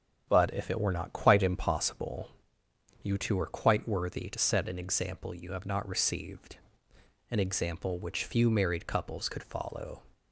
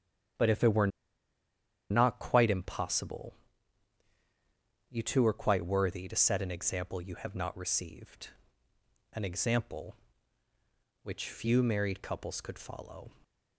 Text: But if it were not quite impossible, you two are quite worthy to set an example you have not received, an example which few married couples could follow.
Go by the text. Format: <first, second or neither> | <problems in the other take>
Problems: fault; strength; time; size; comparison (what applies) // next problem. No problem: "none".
first | starts louder than the rest; strong; until 2.4 s; 9.5 dB; strong in the first // pauses between "were" and "not"; at 0.8 s; 1.0 s long